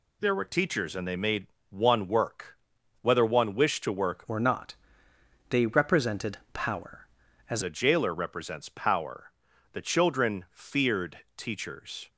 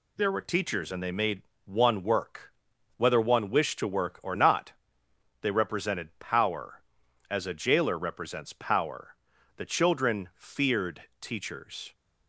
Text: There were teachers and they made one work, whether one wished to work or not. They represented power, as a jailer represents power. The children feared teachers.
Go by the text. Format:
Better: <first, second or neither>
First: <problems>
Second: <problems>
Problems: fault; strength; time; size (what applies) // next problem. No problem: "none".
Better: second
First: pauses between "made" and "one"; slight; at 1.4 s; 0.22 s long // changes voice from "or" to "as"; from 4.2 to 7.6 s; 3.4 s long // pauses between "feared" and "teachers"; slight; at 11.1 s; 0.18 s long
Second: pauses between "made" and "one"; slight; at 1.4 s; 0.22 s long // pauses between "feared" and "teachers"; slight; at 11.0 s; 0.18 s long